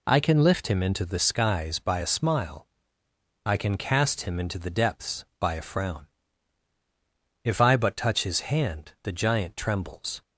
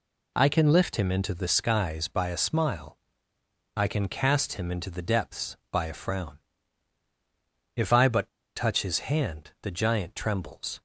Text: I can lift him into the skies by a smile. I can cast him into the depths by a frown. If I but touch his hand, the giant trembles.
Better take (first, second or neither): first